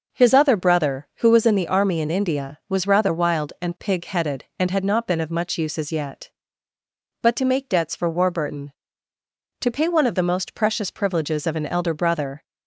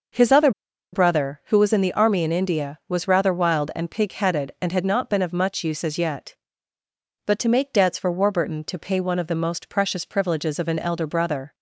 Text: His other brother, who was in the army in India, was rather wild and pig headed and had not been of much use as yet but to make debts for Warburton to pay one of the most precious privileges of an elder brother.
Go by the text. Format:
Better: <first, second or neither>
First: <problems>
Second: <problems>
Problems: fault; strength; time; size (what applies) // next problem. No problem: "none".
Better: first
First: none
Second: pauses between "other" and "brother"; at 0.5 s; 0.42 s long